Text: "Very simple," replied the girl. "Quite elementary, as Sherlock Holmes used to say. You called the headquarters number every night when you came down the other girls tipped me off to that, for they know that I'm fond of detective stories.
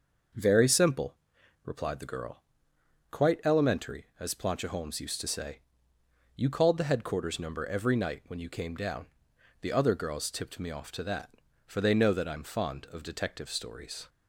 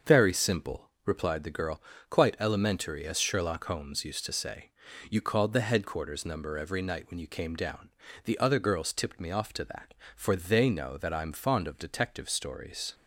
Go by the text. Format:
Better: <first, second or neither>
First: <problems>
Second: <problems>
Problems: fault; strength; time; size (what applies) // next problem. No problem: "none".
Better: second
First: starts louder than the rest; noticeable; until 1.8 s; 6 dB // says "Plancha" for "Sherlock"; at 4.3 s // pauses between "down" and "the"; noticeable; at 9.0 s; 0.54 s long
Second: starts louder than the rest; until 1.2 s; 6.5 dB // pauses between "down" and "the"; slight; at 7.9 s; 0.34 s long